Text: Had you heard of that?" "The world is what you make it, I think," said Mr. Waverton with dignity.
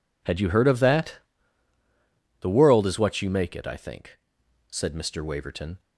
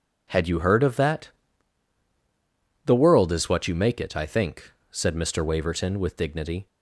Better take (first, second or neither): second